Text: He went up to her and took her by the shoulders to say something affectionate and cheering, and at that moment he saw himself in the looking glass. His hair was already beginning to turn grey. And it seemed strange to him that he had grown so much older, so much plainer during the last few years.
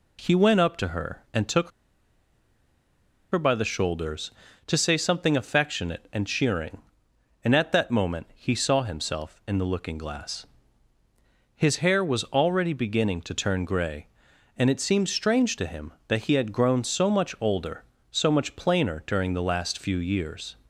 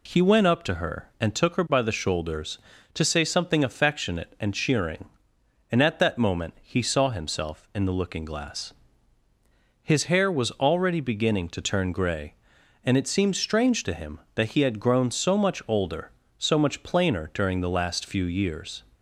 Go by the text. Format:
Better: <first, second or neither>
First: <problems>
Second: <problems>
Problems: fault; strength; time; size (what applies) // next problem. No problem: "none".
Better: second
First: pauses between "took" and "her"; strong; at 1.6 s; 1.6 s long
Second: none